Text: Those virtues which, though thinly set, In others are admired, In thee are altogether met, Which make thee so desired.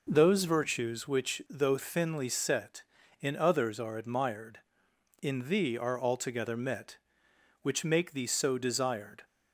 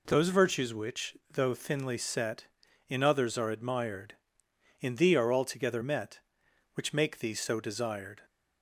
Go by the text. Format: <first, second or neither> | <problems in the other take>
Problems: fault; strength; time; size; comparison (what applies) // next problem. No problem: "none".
neither | none